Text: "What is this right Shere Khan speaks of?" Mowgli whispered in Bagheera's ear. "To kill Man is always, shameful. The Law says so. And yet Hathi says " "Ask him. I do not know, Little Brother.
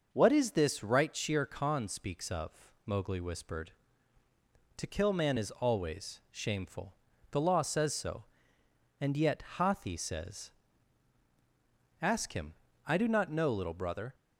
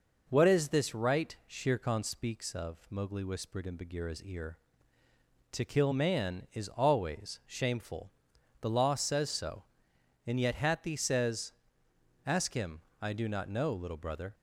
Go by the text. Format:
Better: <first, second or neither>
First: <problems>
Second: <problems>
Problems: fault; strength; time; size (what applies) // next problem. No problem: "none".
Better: second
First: starts louder than the rest; noticeable; until 1.1 s; 6 dB // skips "in Bagheera's ear"; at 4.2 s // pauses between "yet" and "Hathi"; slight; at 9.4 s; 0.16 s long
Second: none